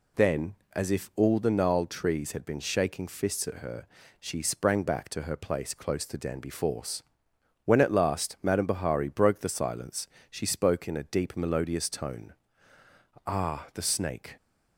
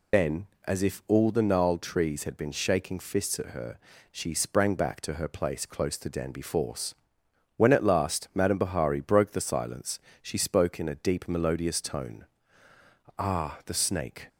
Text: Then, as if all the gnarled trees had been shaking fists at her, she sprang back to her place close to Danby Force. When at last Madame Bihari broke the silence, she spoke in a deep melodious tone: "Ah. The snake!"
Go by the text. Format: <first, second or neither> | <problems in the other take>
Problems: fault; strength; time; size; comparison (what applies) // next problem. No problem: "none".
first | loses the start of "Then"; at 0.1 s; 55 ms